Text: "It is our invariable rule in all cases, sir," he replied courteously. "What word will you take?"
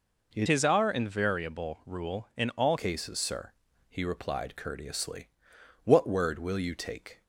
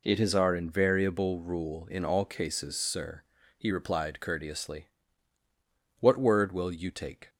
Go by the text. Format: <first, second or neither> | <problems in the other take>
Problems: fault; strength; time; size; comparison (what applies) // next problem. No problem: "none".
second | changes voice from "is" to "all"; from 0.4 to 2.7 s; 2.3 s long